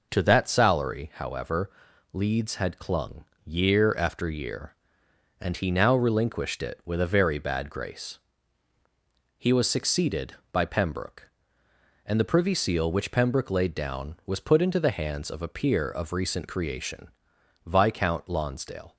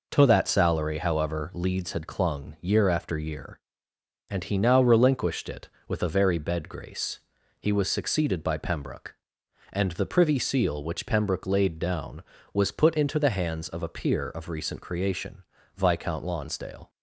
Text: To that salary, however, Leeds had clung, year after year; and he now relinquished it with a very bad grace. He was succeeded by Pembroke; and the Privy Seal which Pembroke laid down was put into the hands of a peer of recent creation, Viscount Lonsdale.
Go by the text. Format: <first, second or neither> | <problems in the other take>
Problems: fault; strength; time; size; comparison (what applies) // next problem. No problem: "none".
first | says "bed" for "bad"; at 6.3 s